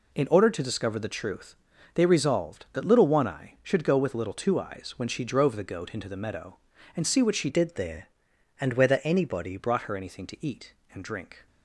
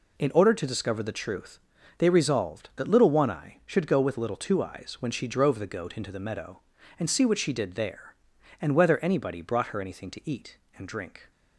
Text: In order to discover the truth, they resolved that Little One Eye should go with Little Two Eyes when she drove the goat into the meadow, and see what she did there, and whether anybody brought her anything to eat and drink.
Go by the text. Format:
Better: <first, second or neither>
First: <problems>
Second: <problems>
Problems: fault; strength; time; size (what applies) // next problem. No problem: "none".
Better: second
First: changes voice from "did" to "anybody"; from 7.4 to 9.5 s; 2.1 s long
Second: none